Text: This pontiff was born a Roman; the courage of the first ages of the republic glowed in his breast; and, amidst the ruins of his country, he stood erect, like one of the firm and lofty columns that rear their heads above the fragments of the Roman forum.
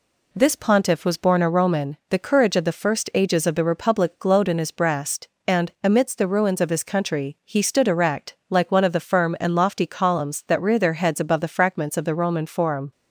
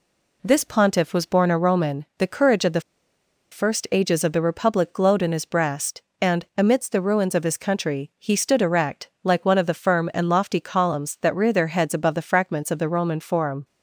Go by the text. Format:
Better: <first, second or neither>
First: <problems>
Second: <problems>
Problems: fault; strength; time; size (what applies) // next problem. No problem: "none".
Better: first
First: none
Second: pauses between "the" and "first"; noticeable; at 2.7 s; 0.71 s long